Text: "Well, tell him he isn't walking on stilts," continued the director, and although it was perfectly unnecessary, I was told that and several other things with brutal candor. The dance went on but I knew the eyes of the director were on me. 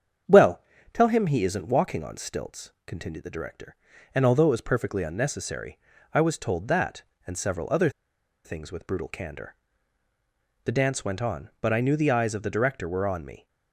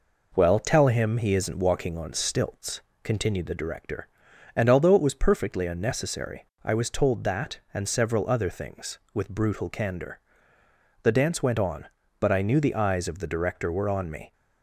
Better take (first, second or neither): second